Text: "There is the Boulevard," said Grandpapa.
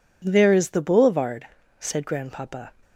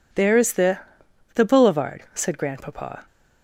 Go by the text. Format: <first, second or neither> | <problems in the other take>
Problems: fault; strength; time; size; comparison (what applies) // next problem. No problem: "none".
first | says "the" twice; at 1.3 s